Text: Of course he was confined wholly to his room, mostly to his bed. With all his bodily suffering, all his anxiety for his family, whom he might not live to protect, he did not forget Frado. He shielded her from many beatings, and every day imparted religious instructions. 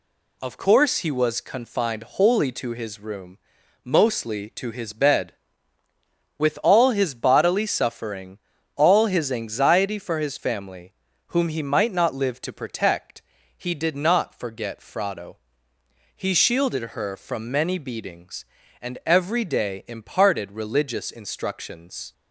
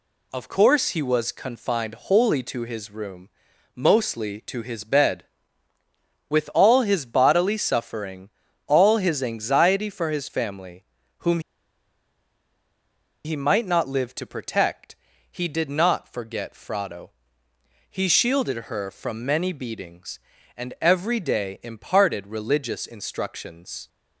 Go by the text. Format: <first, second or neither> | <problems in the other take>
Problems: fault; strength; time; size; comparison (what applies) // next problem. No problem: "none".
first | pauses between "whom" and "he"; strong; at 11.3 s; 1.8 s long